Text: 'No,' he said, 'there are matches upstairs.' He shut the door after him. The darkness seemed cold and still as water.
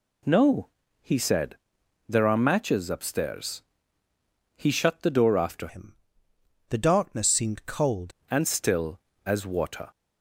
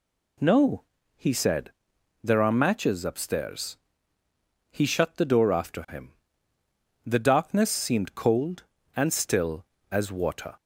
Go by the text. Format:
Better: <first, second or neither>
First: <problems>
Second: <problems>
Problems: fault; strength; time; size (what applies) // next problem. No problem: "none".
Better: second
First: changes voice from "him" to "cold"; from 5.6 to 8.1 s; 2.5 s long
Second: none